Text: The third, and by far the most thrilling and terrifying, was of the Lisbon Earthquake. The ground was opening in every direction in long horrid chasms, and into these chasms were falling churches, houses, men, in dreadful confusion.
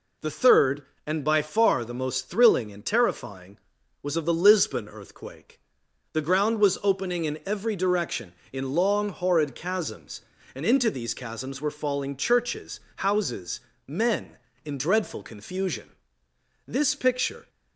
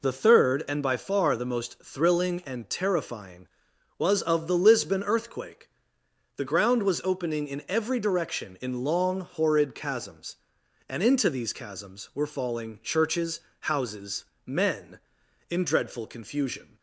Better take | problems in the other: second | goes on to say "This picture"; noticeable; from 16.6 s on; 0.82 s long

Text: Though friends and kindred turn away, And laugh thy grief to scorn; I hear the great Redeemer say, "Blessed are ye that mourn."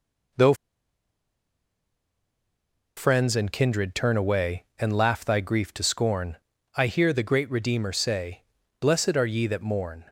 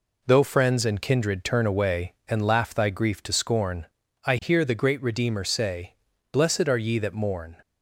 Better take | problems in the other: second | pauses between "Though" and "friends"; strong; at 0.5 s; 2.4 s long

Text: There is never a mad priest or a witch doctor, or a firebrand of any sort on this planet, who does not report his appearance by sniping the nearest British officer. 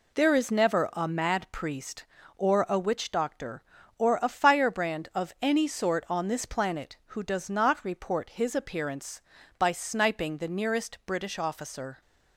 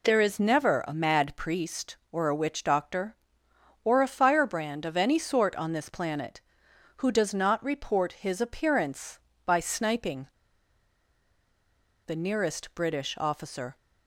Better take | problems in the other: first | pauses between "sniping" and "the"; strong; at 10.2 s; 1.7 s long

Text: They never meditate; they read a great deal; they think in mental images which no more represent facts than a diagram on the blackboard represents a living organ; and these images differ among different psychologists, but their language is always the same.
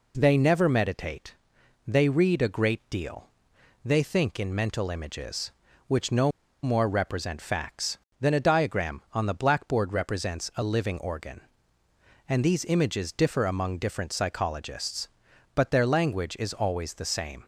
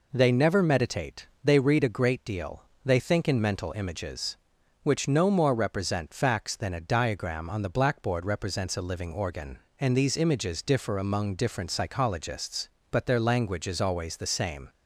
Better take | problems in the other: second | pauses between "no" and "more"; slight; at 6.3 s; 0.33 s long

